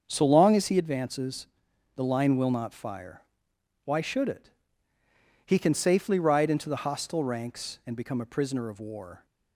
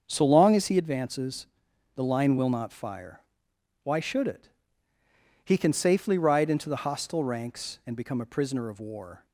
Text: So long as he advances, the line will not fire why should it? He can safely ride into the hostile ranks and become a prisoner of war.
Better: neither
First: starts louder than the rest; until 1.0 s; 7 dB // pauses between "fire" and "why"; noticeable; at 3.2 s; 0.66 s long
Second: starts louder than the rest; until 1.0 s; 7 dB // pauses between "fire" and "why"; noticeable; at 3.1 s; 0.66 s long

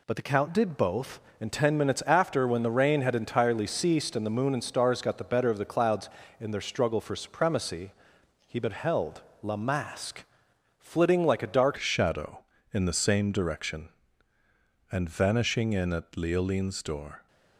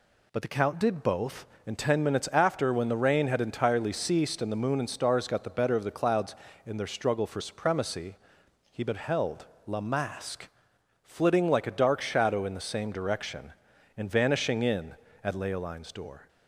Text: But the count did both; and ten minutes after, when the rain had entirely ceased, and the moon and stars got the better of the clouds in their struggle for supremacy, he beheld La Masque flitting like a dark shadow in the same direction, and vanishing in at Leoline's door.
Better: second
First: pauses between "beheld" and "La"; slight; at 9.2 s; 0.20 s long // pauses between "Masque" and "flitting"; noticeable; at 10.2 s; 0.56 s long // changes voice at "shadow"; from 11.7 s on; 5.5 s long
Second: pauses between "beheld" and "La"; slight; at 9.4 s; 0.20 s long // pauses between "Masque" and "flitting"; noticeable; at 10.4 s; 0.56 s long

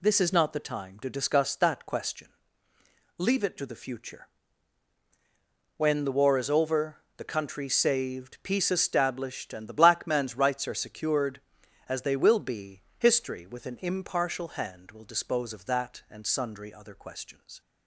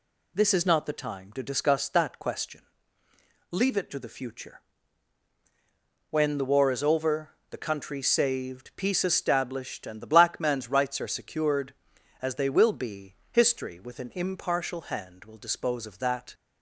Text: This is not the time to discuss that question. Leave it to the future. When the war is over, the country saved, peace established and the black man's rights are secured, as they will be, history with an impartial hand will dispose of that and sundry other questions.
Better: first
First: none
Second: stops before "and sundry other questions"; at 16.3 s

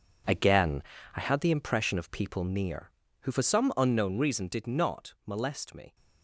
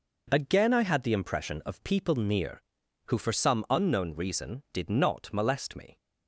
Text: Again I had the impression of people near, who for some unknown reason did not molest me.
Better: second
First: gets quieter; strong; throughout; 11.5 dB // pauses between "Again" and "I"; slight; at 0.8 s; 0.34 s long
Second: none

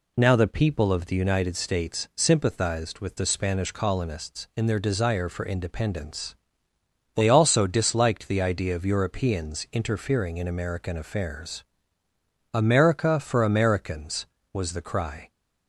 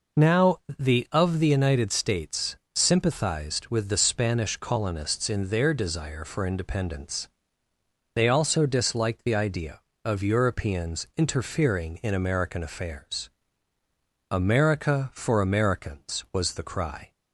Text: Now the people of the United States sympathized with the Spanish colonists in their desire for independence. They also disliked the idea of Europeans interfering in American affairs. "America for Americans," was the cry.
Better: first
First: none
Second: pauses between "Now" and "the"; slight; at 0.5 s; 0.20 s long // skips "people"; at 1.0 s // pauses between "States" and "sympathized"; slight; at 2.5 s; 0.18 s long

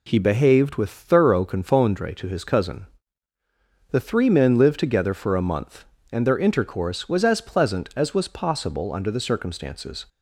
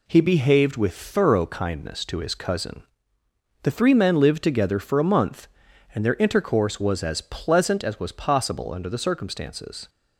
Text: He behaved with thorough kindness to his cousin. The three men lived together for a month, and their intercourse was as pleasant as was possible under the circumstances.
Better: second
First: says "confondre" for "kindness"; at 1.4 s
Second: none

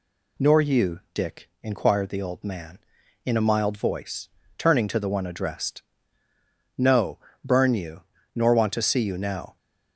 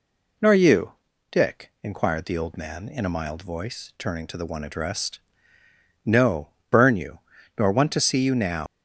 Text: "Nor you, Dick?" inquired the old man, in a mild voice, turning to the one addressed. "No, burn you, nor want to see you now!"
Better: first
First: none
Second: leaves "now" unfinished; at 8.6 s; 110 ms

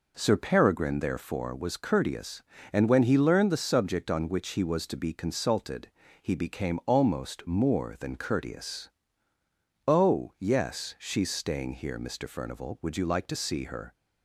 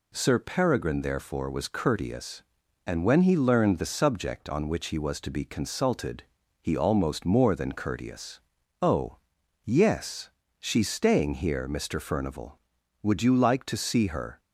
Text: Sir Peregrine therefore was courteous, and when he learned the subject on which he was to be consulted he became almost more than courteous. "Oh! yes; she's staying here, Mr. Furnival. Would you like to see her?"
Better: first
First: pauses between "consulted" and "he"; slight; at 5.8 s; 0.32 s long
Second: pauses between "consulted" and "he"; at 6.2 s; 0.38 s long // skips "became"; at 6.7 s

